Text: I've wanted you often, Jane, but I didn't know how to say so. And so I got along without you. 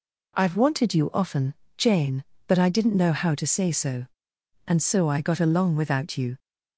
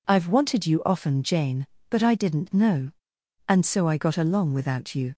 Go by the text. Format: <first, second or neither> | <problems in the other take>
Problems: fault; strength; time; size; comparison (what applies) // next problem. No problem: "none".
first | skips "how to say so"; at 3.1 s